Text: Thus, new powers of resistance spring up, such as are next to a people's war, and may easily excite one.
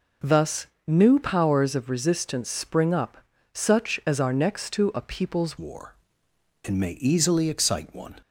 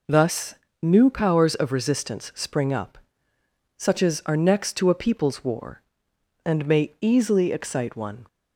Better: second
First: changes voice at "war"; from 5.5 s on; 2.6 s long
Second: none

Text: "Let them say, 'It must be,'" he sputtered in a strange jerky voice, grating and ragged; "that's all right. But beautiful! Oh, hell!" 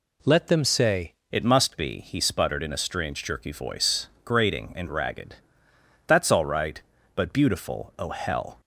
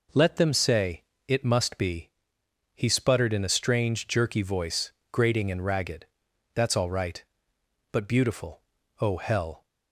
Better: second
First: changes voice at "It"; from 1.3 s on; 7.2 s long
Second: none

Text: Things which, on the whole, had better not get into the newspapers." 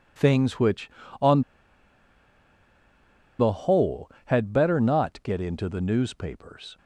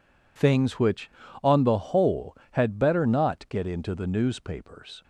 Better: second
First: pauses between "on" and "the"; strong; at 1.4 s; 1.9 s long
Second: none

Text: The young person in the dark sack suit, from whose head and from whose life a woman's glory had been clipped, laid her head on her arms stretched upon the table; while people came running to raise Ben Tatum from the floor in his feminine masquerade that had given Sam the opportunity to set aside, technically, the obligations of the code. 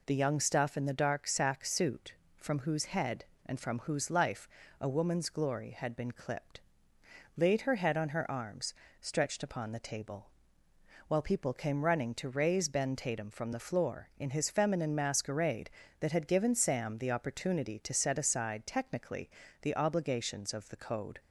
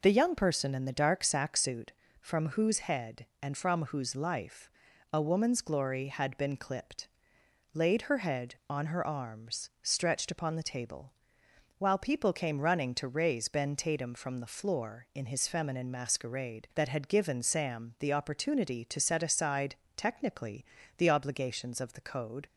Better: second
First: says "stuff" for "person"; at 0.3 s // pauses between "life" and "a"; slight; at 4.4 s; 0.32 s long // pauses between "arms" and "stretched"; slight; at 8.7 s; 0.26 s long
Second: pauses between "life" and "a"; at 4.6 s; 0.42 s long

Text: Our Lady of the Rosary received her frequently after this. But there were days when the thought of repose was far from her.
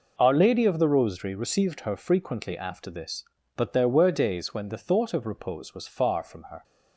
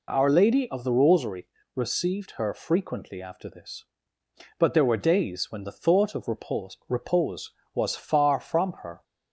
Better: first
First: none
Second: pauses between "Rosary" and "received"; slight; at 1.4 s; 0.30 s long // says "repose" twice; at 6.8 s

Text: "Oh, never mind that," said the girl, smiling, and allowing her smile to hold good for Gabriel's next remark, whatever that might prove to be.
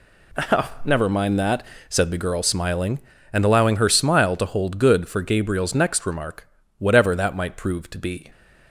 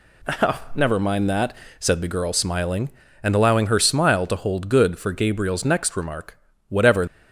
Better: first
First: none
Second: stops before "that might prove to be"; at 7.0 s

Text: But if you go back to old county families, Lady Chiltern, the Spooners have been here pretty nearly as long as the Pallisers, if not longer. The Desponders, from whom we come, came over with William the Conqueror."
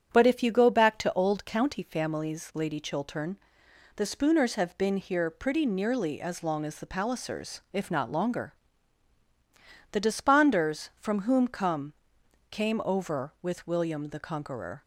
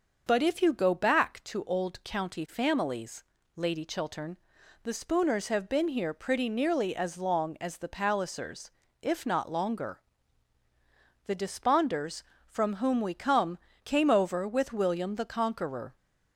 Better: second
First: starts louder than the rest; strong; until 1.1 s; 9 dB // skips "we"; at 11.4 s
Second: starts louder than the rest; until 1.2 s; 6.5 dB

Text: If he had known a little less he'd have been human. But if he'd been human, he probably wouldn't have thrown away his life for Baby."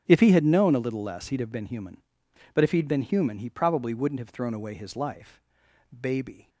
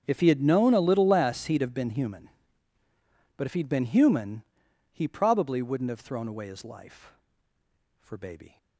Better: second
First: starts louder than the rest; strong; until 1.0 s; 7.5 dB // skips "for"; at 5.6 s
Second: starts louder than the rest; strong; until 1.0 s; 7.5 dB

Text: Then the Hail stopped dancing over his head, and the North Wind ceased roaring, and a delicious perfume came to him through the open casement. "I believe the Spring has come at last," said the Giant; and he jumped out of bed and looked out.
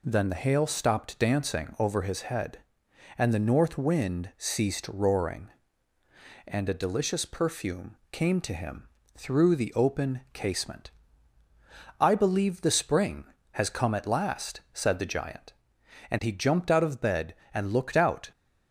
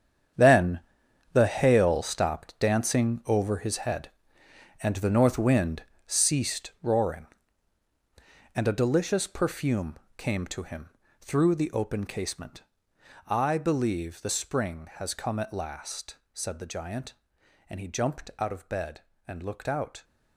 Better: first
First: pauses between "him" and "through"; slight; at 8.8 s; 0.30 s long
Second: gets quieter; strong; throughout; 12 dB // pauses between "Then" and "the"; noticeable; at 0.7 s; 0.54 s long // pauses between "Wind" and "ceased"; slight; at 5.8 s; 0.24 s long // pauses between "perfume" and "came"; slight; at 9.9 s; 0.22 s long // pauses between "him" and "through"; slight; at 10.8 s; 0.32 s long

